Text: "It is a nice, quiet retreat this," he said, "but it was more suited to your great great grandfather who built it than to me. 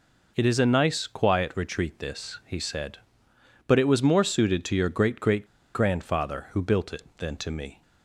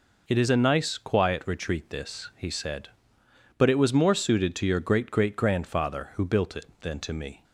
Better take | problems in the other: second | pauses between "great" and "grandfather"; slight; at 5.4 s; 0.29 s long

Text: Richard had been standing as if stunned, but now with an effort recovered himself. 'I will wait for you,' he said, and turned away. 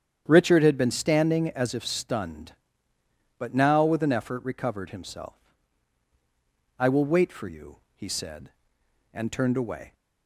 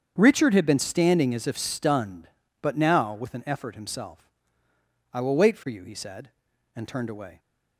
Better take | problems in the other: first | starts louder than the rest; strong; until 1.1 s; 7.5 dB; strong in the first // skips "recovered"; at 3.7 s

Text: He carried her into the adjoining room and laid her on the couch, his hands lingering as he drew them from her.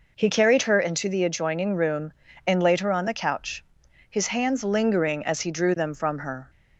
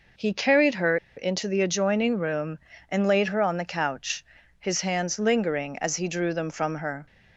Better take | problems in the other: first | pauses between "her" and "into"; slight; at 0.9 s; 0.20 s long

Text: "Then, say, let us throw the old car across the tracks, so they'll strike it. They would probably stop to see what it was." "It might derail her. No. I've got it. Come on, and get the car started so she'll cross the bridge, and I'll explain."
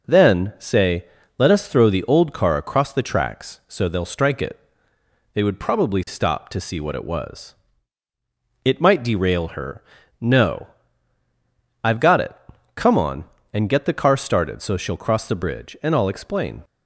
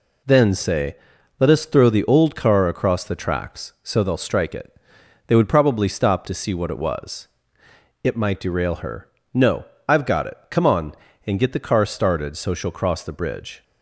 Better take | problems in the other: first | stops before "and I'll explain"; at 13.6 s

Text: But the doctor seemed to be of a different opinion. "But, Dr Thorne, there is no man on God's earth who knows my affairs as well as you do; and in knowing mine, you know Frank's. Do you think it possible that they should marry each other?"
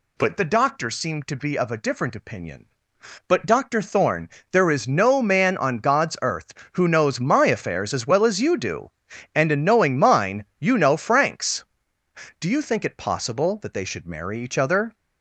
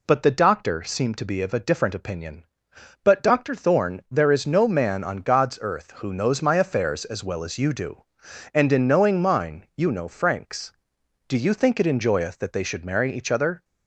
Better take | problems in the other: first | says "enjoyeth" for "possible"; at 11.8 s

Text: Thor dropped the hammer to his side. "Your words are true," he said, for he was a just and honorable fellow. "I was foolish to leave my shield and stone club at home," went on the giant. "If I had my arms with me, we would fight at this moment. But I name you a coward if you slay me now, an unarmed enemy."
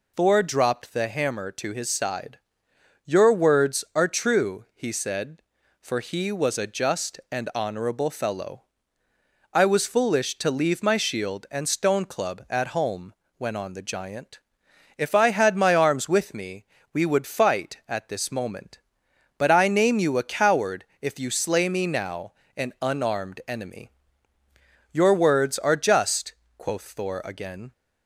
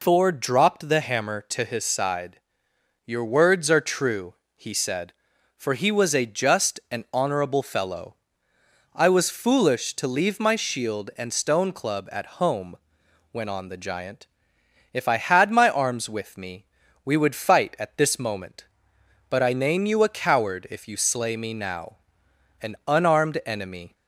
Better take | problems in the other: second | pauses between "coward" and "if"; slight; at 20.8 s; 0.16 s long // goes on to say "Your words are just quoth Thor again"; strong; from 24.9 s on; 2.8 s long

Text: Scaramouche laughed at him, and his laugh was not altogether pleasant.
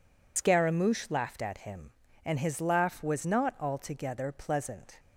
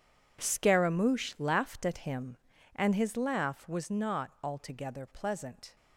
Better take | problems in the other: second | loses the start of "Scaramouche"; at 0.3 s; 90 ms

